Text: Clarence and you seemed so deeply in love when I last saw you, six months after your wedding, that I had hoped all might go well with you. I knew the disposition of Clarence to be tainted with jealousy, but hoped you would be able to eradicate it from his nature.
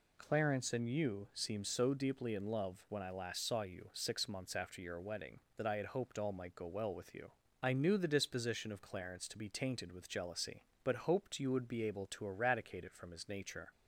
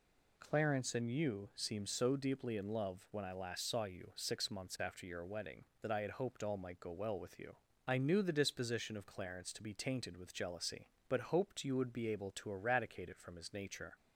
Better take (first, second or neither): neither